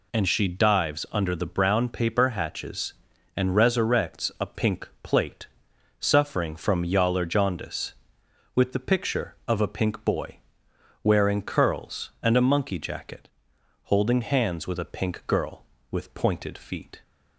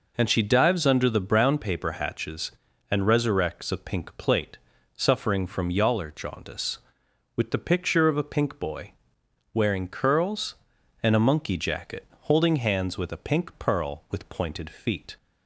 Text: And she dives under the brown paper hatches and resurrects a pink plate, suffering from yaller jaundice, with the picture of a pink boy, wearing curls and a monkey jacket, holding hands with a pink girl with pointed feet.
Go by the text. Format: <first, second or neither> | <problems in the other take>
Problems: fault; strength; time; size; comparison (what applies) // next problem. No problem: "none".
first | says "pearl" for "girl"; at 13.5 s